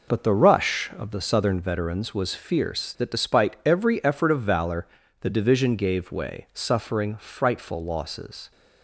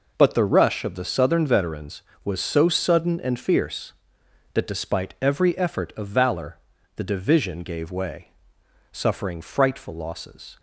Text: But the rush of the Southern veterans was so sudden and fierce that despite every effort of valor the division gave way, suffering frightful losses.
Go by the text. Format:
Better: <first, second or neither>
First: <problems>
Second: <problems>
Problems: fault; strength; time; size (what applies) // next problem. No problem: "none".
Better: second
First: skips "so sudden and"; at 2.3 s // pauses between "valor" and "the"; slight; at 4.8 s; 0.36 s long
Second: pauses between "valor" and "the"; at 6.5 s; 0.40 s long